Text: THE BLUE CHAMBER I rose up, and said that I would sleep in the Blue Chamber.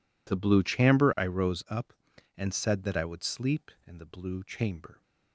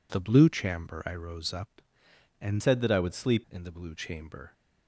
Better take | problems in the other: first | changes voice from "said" to "sleep"; from 2.5 to 3.4 s; 0.9 s long

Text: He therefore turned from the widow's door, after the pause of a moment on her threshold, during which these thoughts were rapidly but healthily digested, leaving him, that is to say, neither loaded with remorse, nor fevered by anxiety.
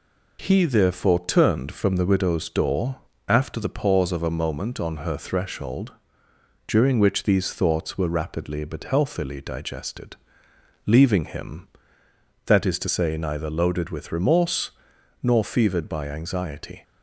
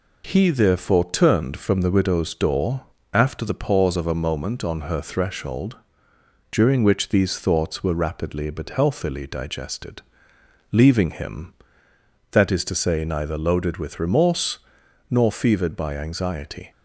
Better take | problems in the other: neither | none

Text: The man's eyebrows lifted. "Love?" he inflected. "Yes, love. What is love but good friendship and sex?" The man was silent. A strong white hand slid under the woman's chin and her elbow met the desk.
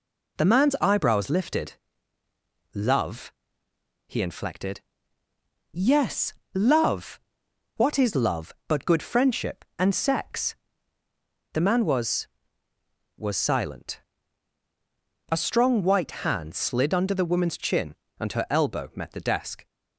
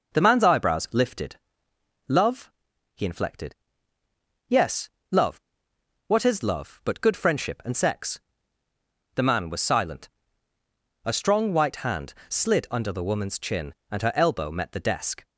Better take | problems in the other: second | says "was" twice; at 13.1 s

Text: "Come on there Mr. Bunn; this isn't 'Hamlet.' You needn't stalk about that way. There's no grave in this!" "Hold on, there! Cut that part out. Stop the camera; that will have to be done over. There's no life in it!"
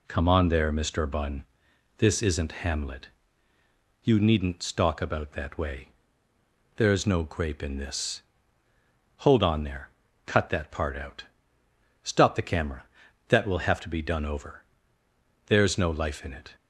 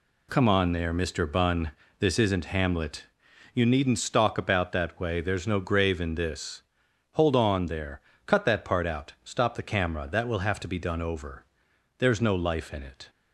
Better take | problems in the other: second | says "grape" for "grave"; at 7.2 s

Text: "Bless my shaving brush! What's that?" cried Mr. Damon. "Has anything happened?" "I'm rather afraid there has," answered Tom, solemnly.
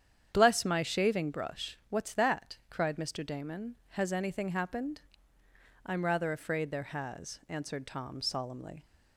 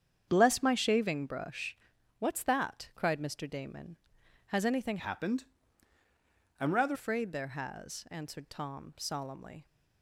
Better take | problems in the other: first | starts louder than the rest; strong; until 1.2 s; 8 dB; strong in the first // changes voice from "happened" to "rather"; from 4.9 to 6.9 s; 2.0 s long

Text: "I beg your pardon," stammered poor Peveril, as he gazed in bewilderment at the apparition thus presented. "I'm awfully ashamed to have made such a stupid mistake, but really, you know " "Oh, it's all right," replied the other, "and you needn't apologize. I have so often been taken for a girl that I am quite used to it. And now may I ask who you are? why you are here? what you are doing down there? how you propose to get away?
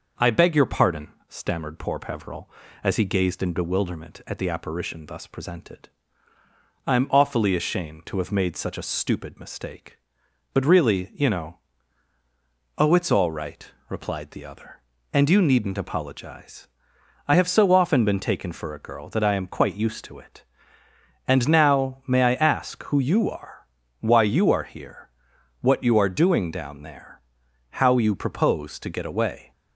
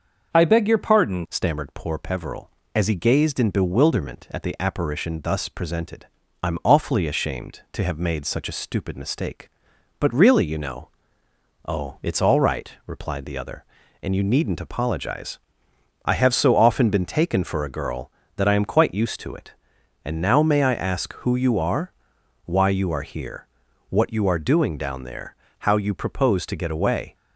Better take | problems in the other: first | starts louder than the rest; until 1.3 s; 6.5 dB // changes voice at "stammered"; from 1.3 s on; 25.8 s long

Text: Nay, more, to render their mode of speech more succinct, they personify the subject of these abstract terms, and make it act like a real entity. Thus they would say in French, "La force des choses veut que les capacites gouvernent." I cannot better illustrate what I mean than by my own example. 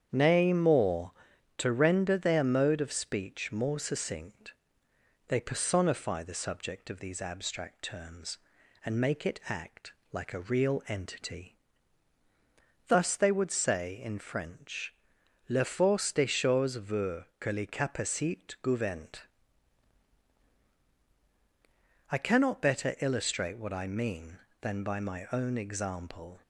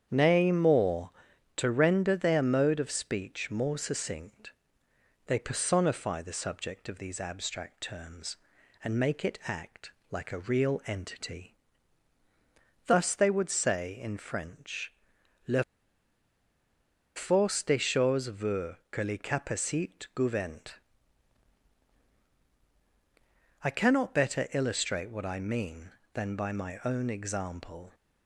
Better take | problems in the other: first | starts louder than the rest; strong; until 1.1 s; 8.5 dB; strong in the first // pauses between "act" and "like"; slight; at 9.9 s; 0.20 s long; slight in the first // pauses between "La" and "force"; strong; at 15.6 s; 1.5 s long

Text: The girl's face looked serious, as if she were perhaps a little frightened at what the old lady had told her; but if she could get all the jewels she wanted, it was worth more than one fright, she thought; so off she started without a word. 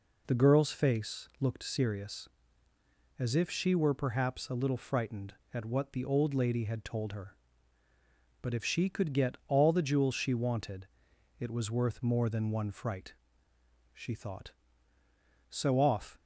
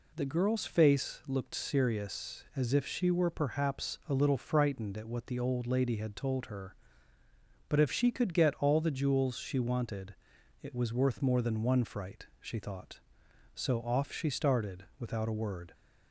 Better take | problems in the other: second | stops before "she started without a word"; at 16.1 s

